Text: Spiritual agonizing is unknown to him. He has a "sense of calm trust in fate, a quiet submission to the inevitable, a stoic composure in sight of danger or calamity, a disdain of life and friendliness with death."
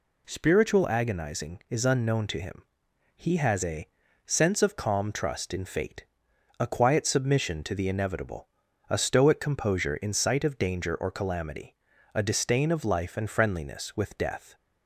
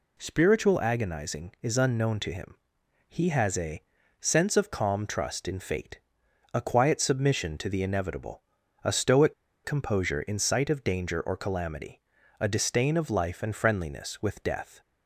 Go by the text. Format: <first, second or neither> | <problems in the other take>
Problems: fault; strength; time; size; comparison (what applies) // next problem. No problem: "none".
first | pauses between "a" and "sense"; at 3.8 s; 0.38 s long; also in the first // pauses between "stoic" and "composure"; slight; at 9.3 s; 0.32 s long